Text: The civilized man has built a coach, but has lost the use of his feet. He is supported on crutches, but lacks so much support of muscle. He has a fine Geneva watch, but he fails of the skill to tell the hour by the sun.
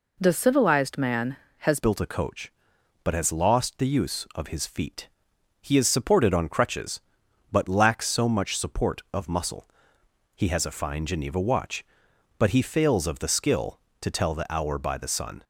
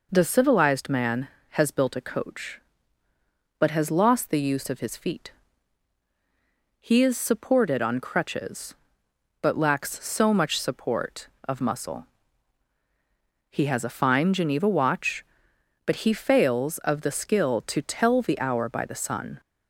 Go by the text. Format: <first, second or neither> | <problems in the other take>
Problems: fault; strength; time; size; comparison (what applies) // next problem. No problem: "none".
second | changes voice at "built"; from 1.7 s on; 13.7 s long